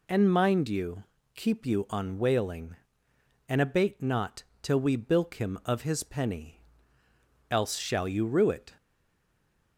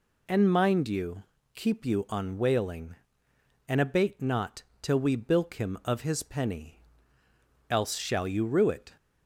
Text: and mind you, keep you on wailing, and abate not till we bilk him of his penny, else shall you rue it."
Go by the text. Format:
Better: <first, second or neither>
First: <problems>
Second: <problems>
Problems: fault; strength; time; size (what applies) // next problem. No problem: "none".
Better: second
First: pauses between "not" and "till"; slight; at 4.4 s; 0.18 s long // stays silent after the last word; from 8.7 s on; 1.0 s long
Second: pauses between "not" and "till"; slight; at 4.6 s; 0.18 s long